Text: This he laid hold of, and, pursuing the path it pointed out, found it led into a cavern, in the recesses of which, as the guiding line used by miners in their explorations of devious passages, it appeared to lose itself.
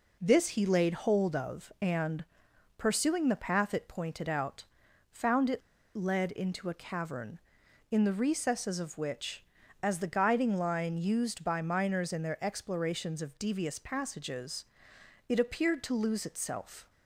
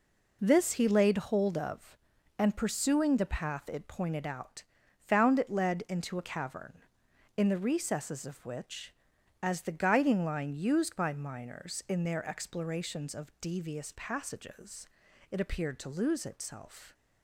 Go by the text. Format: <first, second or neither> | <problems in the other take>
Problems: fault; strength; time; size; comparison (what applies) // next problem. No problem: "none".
second | pauses between "it" and "led"; slight; at 5.6 s; 0.34 s long